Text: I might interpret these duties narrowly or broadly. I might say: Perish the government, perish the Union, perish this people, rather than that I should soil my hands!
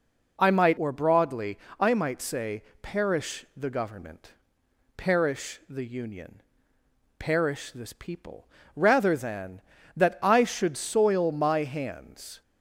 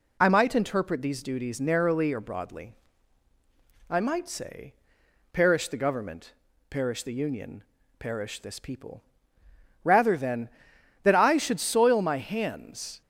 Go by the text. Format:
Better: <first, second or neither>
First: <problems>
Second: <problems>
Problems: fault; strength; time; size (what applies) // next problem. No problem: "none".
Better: second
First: skips "interpret these duties narrowly"; at 0.7 s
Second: none